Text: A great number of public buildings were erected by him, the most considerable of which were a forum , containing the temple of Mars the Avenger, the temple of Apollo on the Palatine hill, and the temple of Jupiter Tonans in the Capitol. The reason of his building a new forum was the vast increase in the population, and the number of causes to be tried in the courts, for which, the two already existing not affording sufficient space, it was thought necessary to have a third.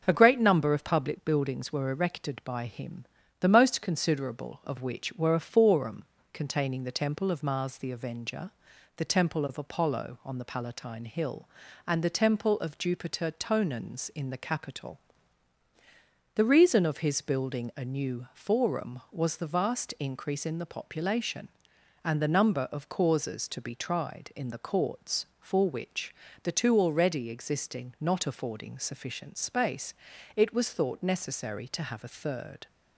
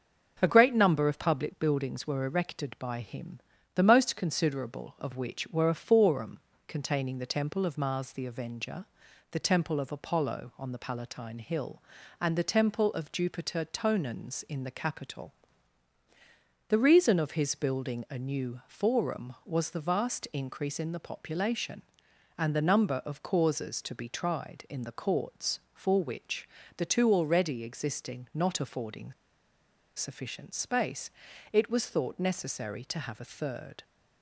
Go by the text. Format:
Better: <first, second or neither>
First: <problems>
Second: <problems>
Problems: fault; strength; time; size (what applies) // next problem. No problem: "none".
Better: first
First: starts louder than the rest; until 1.0 s; 6 dB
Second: starts louder than the rest; until 1.4 s; 6 dB // pauses between "affording" and "sufficient"; noticeable; at 29.1 s; 0.84 s long